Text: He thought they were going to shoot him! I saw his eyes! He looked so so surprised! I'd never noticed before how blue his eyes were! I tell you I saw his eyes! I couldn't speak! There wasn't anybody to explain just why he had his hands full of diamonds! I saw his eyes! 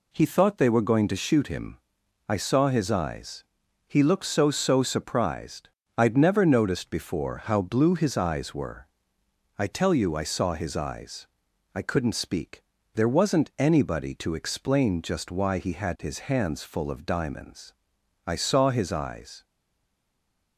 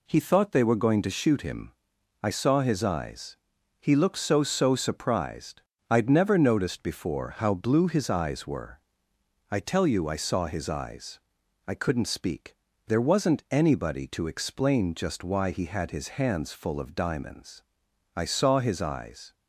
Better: second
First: stays silent after the last word; from 19.4 s on; 1.1 s long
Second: none

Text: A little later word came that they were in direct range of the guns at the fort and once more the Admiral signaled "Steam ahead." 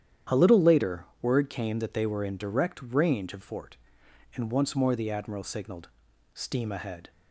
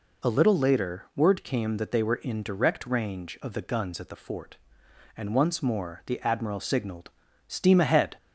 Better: second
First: starts louder than the rest; strong; until 1.4 s; 10 dB // pauses between "later" and "word"; slight; at 1.0 s; 0.16 s long // skips "the guns at the"; at 3.4 s // pauses between "signaled" and "Steam"; at 5.8 s; 0.44 s long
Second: pauses between "signaled" and "Steam"; at 7.1 s; 0.38 s long

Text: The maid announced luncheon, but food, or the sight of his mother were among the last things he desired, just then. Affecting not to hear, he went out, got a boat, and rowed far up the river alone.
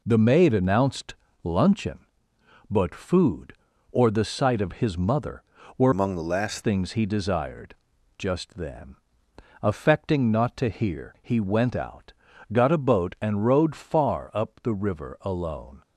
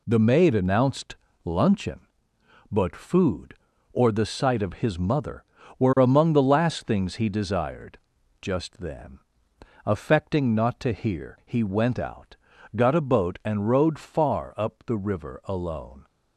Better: second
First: pauses between "announced" and "luncheon"; slight; at 1.1 s; 0.30 s long // changes voice from "among" to "last"; from 5.9 to 6.6 s; 0.7 s long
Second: pauses between "announced" and "luncheon"; slight; at 1.1 s; 0.30 s long

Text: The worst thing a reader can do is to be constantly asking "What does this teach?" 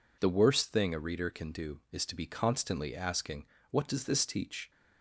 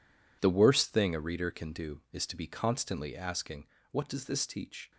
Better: first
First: pauses between "asking" and "What"; slight; at 3.4 s; 0.26 s long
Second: gets quieter; strong; throughout; 12.5 dB // pauses between "asking" and "What"; slight; at 3.6 s; 0.26 s long

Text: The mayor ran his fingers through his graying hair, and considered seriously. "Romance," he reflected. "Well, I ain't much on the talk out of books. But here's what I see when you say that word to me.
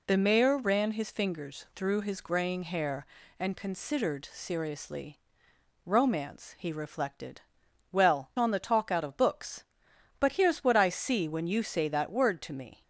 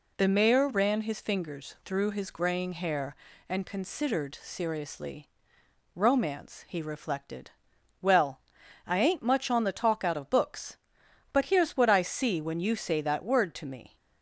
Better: second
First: skips "I ain't much"; at 8.3 s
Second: none

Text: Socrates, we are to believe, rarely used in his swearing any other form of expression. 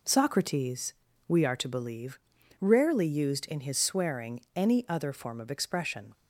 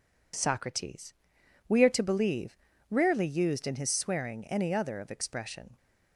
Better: first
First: none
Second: skips "form"; at 4.9 s

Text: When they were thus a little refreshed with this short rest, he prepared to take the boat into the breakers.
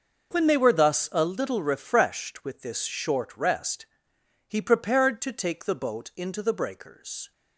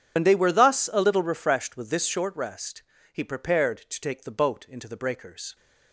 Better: first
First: none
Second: loses the start of "When"; at 0.1 s; 70 ms

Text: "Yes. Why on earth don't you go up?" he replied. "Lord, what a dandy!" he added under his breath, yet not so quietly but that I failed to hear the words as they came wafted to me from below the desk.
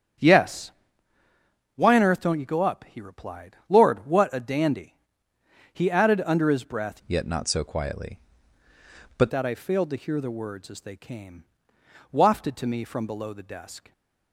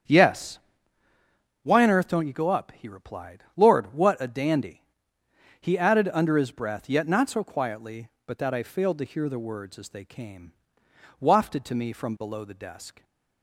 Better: second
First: starts louder than the rest; strong; until 2.2 s; 8.5 dB // changes voice from "yet" to "but"; from 7.0 to 9.2 s; 2.2 s long // pauses between "came" and "wafted"; noticeable; at 11.4 s; 0.66 s long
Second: starts louder than the rest; strong; until 2.1 s; 8 dB // pauses between "came" and "wafted"; noticeable; at 10.5 s; 0.66 s long

